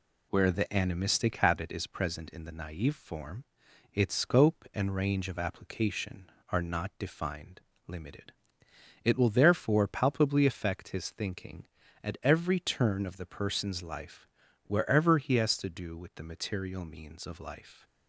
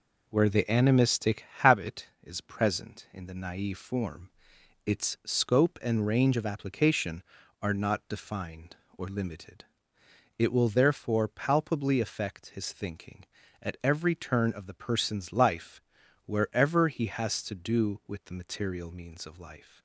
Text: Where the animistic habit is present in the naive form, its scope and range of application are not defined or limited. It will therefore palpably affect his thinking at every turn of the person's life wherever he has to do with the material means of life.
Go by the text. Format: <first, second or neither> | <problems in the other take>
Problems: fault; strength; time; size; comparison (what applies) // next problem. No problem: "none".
second | skips "or"; at 7.7 s // pauses between "life" and "wherever"; at 14.2 s; 0.38 s long; also in the second